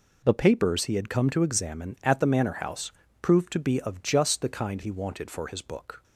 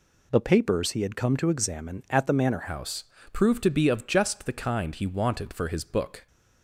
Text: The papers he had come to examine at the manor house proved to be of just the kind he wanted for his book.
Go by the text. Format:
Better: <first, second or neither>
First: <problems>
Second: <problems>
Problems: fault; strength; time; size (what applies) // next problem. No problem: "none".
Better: first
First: pauses between "house" and "proved"; slight; at 2.9 s; 0.30 s long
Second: changes voice at "house"; from 2.6 s on; 3.6 s long // pauses between "house" and "proved"; slight; at 3.0 s; 0.28 s long